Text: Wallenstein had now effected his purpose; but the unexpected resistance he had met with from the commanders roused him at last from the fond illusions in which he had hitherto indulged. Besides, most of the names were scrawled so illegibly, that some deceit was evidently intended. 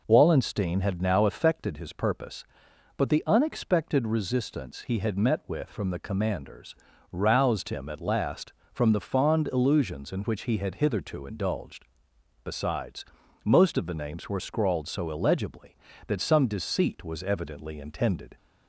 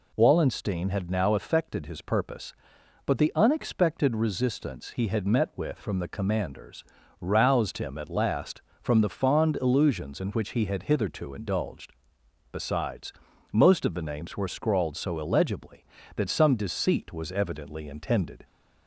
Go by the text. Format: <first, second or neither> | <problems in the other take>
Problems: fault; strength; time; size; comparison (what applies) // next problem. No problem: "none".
second | starts louder than the rest; noticeable; until 1.8 s; 5 dB // pauses between "commanders" and "roused"; slight; at 6.7 s; 0.36 s long; slight in the second